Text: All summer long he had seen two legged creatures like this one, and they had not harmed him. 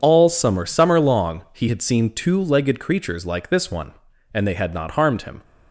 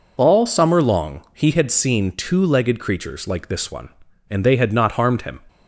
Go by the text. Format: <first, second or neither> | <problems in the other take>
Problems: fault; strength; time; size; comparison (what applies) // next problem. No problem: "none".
second | says "summer" twice; at 0.6 s